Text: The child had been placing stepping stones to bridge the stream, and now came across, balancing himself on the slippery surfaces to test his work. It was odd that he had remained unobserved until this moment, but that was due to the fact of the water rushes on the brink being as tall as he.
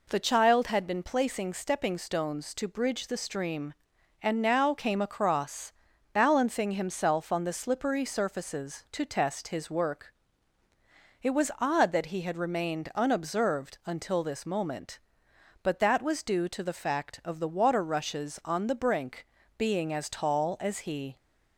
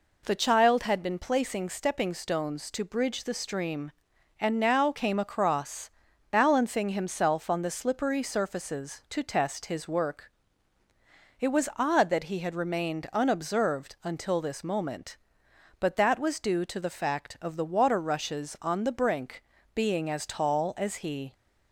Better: neither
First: pauses between "brink" and "being"; slight; at 19.2 s; 0.32 s long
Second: pauses between "brink" and "being"; slight; at 19.4 s; 0.32 s long

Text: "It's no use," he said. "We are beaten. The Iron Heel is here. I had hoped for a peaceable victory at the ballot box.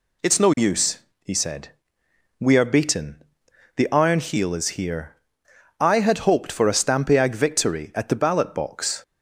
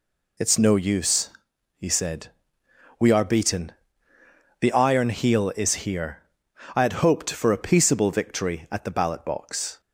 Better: second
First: says "stampiag" for "peaceable"; at 6.7 s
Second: none

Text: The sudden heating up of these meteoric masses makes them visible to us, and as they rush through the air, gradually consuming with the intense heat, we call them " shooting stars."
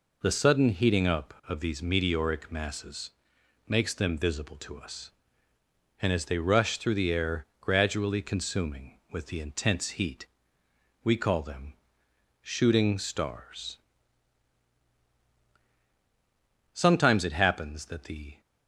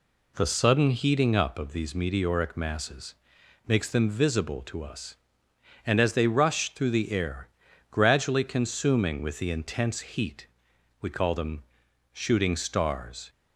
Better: second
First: pauses between "masses" and "makes"; noticeable; at 3.1 s; 0.54 s long // goes on to say "Sometimes it happens that the"; from 16.7 s on; 1.6 s long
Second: pauses between "masses" and "makes"; noticeable; at 3.1 s; 0.54 s long

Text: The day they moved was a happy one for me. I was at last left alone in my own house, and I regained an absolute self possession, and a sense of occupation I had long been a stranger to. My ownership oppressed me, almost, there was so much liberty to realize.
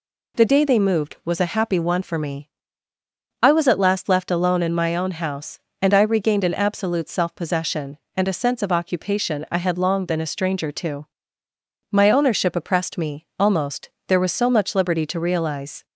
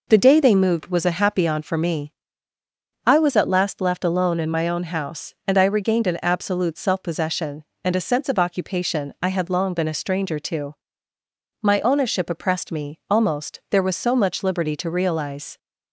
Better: first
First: none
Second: says "on" for "one"; at 1.4 s

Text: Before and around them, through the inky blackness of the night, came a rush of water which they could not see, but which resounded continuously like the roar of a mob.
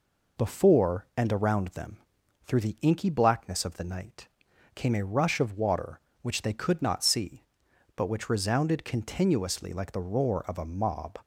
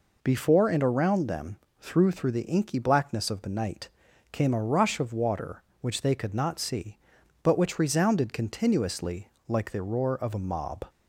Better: first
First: none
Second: says "through" twice; at 2.0 s // pauses between "continuously" and "like"; slight; at 9.2 s; 0.20 s long

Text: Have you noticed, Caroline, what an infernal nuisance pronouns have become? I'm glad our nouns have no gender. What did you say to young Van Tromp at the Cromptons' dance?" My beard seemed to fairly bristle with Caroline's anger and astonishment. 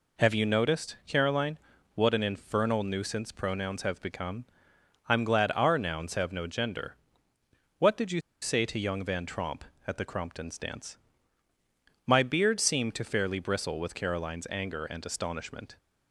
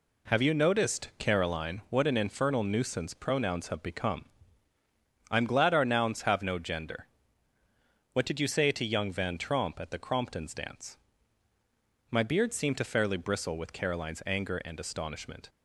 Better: second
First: pauses between "you" and "say"; slight; at 8.2 s; 0.21 s long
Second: none

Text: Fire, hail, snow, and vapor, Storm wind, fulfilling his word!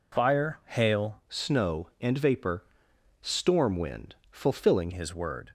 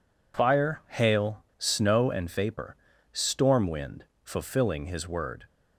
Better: second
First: changes voice from "snow" to "fulfilling"; from 1.2 to 4.9 s; 3.7 s long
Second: none

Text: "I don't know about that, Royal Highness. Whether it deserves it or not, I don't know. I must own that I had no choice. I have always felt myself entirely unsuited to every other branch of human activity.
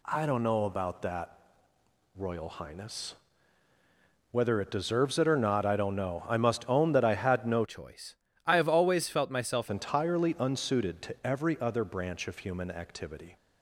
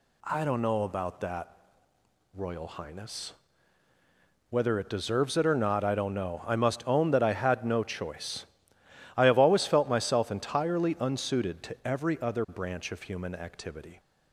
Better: second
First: changes voice from "choice" to "myself"; from 7.6 to 9.6 s; 2.0 s long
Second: none

